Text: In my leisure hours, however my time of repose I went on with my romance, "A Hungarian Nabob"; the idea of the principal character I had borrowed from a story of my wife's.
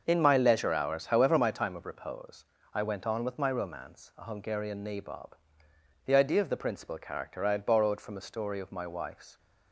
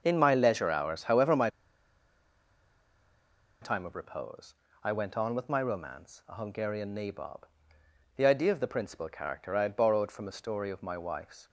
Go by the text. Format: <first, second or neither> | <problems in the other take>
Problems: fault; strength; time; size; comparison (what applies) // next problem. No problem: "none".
first | starts louder than the rest; noticeable; until 1.0 s; 6 dB; noticeable in the first // pauses between "my" and "time"; strong; at 1.4 s; 2.1 s long // pauses between "repose" and "I"; slight; at 4.5 s; 0.30 s long; slight in the first